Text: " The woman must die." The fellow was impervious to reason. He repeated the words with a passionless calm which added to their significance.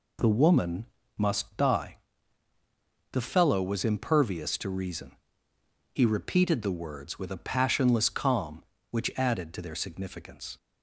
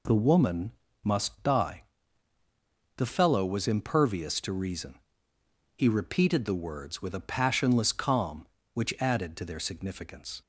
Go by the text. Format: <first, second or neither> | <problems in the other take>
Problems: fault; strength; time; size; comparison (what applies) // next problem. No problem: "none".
neither | pauses between "woman" and "must"; slight; the same in both